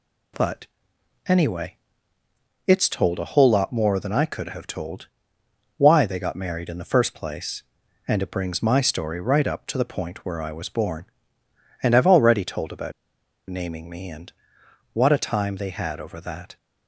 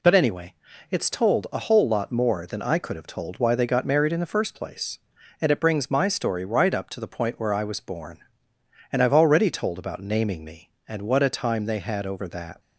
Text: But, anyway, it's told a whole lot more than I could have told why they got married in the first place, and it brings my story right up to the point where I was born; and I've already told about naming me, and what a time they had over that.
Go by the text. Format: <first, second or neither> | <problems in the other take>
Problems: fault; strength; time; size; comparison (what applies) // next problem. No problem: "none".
second | pauses between "told" and "why"; noticeable; at 5.0 s; 0.70 s long // pauses between "about" and "naming"; noticeable; at 12.9 s; 0.58 s long // pauses between "and" and "what"; noticeable; at 14.3 s; 0.60 s long